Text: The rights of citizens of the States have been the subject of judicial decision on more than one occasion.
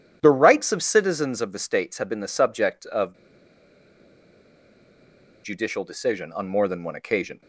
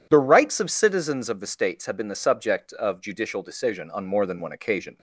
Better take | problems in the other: second | pauses between "of" and "judicial"; strong; at 3.1 s; 2.2 s long

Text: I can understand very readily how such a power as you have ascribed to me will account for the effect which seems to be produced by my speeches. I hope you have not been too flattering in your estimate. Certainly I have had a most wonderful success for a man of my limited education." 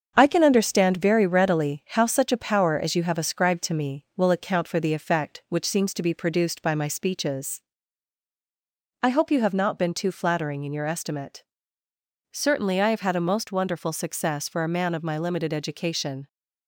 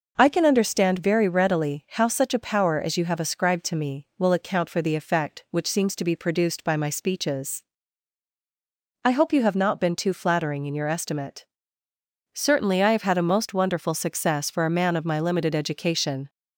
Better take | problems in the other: second | gets quieter; noticeable; throughout; 4.5 dB

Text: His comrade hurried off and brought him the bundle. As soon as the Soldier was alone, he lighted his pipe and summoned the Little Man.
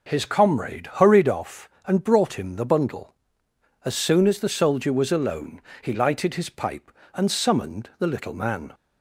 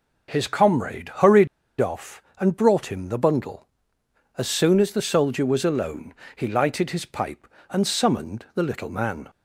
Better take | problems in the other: first | pauses between "hurried" and "off"; slight; at 1.4 s; 0.32 s long

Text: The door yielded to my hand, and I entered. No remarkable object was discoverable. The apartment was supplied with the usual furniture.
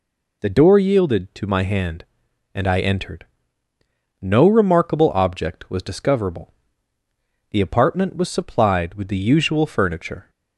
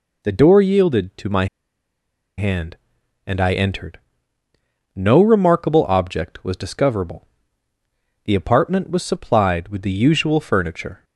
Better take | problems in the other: first | pauses between "my" and "hand"; noticeable; at 1.4 s; 0.91 s long

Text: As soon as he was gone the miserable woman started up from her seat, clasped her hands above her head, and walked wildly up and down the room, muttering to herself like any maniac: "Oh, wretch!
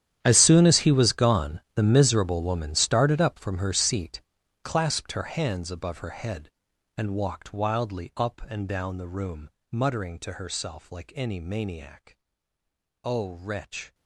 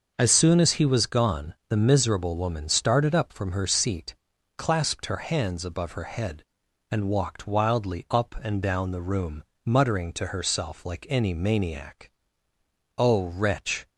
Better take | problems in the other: second | gets quieter; strong; throughout; 18.5 dB // starts louder than the rest; strong; until 1.2 s; 10.5 dB; noticeable in the second

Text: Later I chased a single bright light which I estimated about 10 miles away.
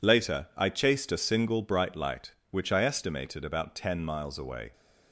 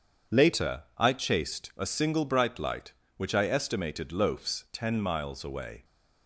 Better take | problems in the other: first | starts louder than the rest; strong; until 1.4 s; 7.5 dB // says "loafs" for "about"; at 4.1 s

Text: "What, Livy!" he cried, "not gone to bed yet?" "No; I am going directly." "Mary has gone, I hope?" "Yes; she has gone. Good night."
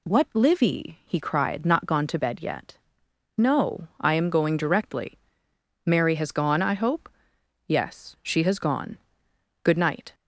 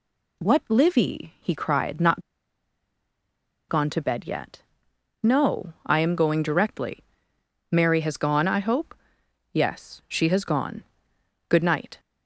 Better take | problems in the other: first | pauses between "not" and "gone"; strong; at 2.2 s; 1.4 s long

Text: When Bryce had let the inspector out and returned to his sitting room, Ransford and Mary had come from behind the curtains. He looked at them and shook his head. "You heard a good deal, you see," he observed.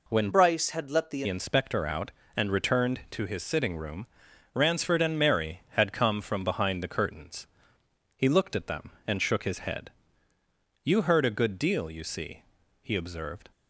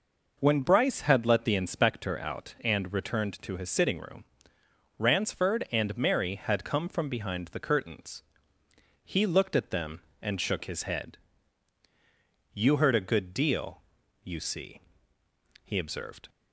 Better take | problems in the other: second | changes voice from "Bryce" to "the"; from 0.3 to 1.2 s; 0.9 s long

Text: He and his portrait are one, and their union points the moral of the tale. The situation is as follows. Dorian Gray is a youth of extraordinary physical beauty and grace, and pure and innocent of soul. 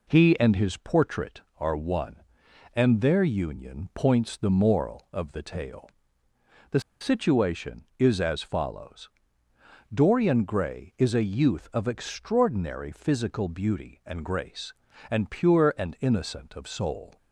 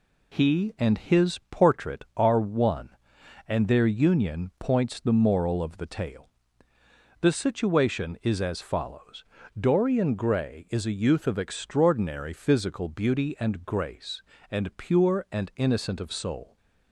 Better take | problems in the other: second | pauses between "The" and "situation"; slight; at 6.8 s; 0.20 s long

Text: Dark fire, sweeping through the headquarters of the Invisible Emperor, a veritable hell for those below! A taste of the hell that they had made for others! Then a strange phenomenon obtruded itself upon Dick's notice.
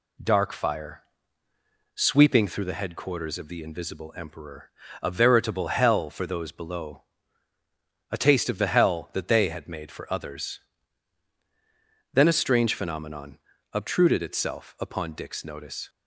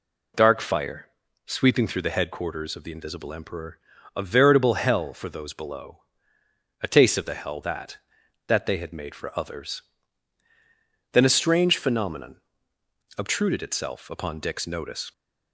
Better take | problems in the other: first | says "that" twice; at 8.4 s // pauses between "phenomenon" and "obtruded"; noticeable; at 12.3 s; 0.78 s long; slight in the first

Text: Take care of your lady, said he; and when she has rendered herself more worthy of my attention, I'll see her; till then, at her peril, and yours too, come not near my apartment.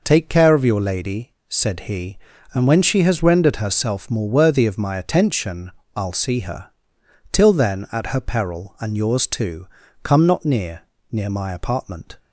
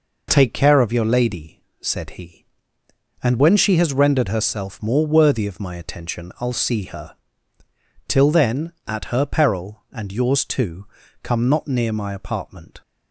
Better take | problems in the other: second | says "near" twice; at 11.1 s

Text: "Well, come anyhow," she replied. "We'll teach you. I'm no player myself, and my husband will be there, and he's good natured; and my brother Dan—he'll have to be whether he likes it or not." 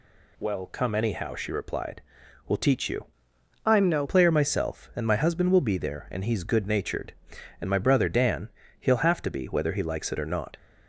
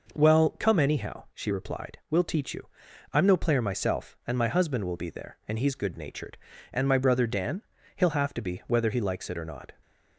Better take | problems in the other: second | changes voice from "I'm" to "no"; from 3.6 to 4.0 s; 0.4 s long

